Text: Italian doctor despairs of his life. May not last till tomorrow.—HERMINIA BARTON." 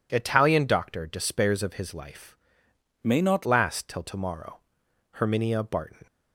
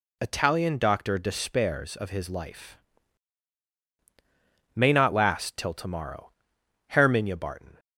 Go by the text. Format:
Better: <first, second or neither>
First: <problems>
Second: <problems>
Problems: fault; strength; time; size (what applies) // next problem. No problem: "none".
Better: second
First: changes voice from "May" to "not"; from 3.0 to 3.4 s; 0.4 s long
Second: none